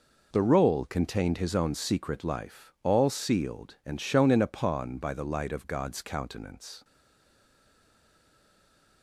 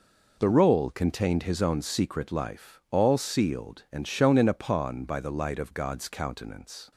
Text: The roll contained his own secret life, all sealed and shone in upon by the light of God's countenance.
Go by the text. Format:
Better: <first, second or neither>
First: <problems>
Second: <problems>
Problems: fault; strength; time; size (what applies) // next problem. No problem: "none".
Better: second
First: stays silent after the last word; from 6.8 s on; 2.2 s long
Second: none